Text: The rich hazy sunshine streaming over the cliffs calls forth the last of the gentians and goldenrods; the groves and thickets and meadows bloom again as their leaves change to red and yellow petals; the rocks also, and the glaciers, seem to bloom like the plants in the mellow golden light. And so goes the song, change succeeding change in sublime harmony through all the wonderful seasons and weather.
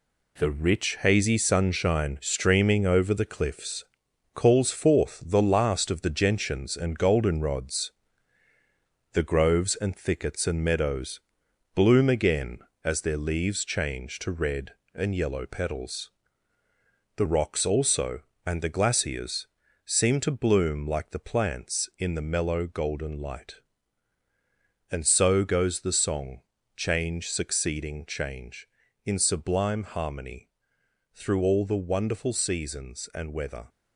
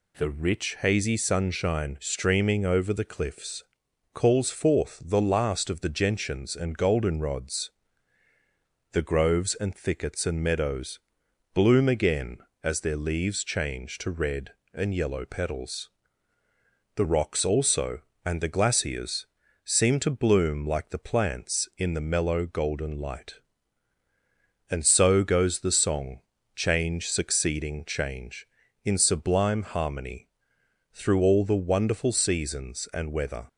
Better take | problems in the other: second | gets quieter; throughout; 6.5 dB // pauses between "cliffs" and "calls"; noticeable; at 3.8 s; 0.50 s long; noticeable in the second // pauses between "meadows" and "bloom"; noticeable; at 11.2 s; 0.54 s long; noticeable in the second // pauses between "harmony" and "through"; noticeable; at 30.4 s; 0.66 s long; noticeable in the second

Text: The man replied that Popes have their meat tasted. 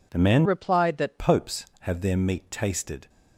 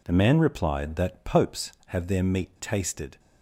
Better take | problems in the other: second | changes voice from "replied" to "that"; from 0.4 to 1.1 s; 0.7 s long

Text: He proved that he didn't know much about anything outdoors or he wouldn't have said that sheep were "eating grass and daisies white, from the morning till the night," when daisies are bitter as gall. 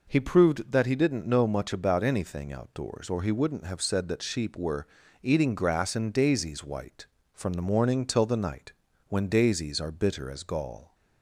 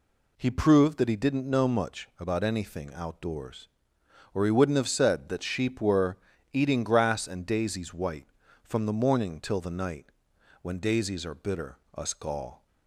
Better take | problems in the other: first | pauses between "were" and "eating"; slight; at 6.1 s; 0.34 s long; slight in the first // says "us" for "as"; at 11.9 s

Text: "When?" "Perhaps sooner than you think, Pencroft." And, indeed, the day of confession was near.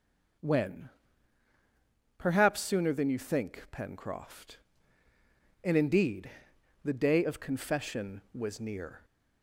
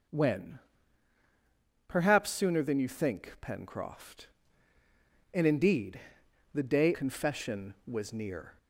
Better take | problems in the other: first | skips "of"; at 6.9 s

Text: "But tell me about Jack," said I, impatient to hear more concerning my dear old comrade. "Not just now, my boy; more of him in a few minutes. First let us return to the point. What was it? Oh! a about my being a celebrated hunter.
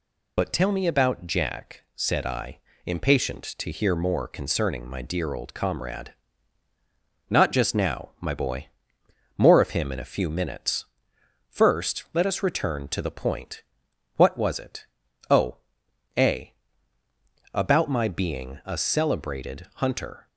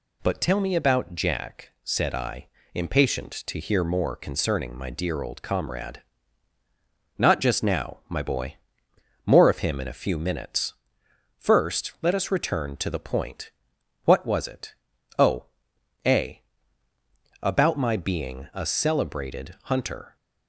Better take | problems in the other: second | loses the start of "But"; at 0.3 s; 45 ms // pauses between "a" and "about"; at 16.5 s; 1.0 s long; also in the second

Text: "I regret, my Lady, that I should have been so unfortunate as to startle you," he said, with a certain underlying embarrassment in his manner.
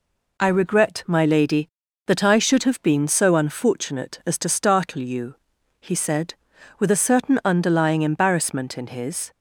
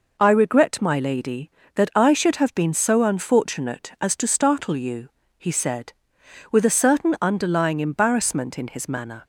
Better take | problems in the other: second | stops before "manner"; at 9.3 s

